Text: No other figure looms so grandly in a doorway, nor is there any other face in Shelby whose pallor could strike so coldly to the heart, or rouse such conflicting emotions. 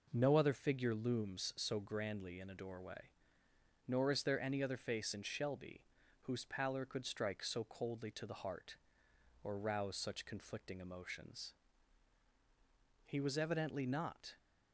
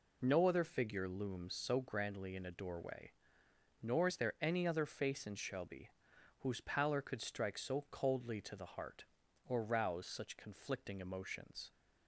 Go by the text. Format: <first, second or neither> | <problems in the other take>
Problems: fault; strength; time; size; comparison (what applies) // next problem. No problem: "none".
second | pauses between "Shelby" and "whose"; at 5.8 s; 0.40 s long; noticeable in the second // goes on to say "He was evidently not"; from 13.0 s on; 1.3 s long